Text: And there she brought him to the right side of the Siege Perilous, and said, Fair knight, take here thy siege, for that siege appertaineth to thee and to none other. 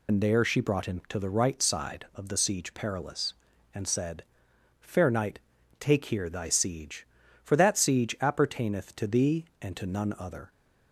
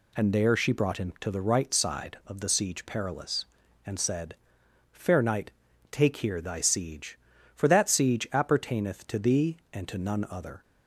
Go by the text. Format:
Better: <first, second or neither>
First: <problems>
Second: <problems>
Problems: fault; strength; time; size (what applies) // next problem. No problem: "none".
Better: second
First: loses the start of "And"; at 0.0 s; 60 ms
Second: none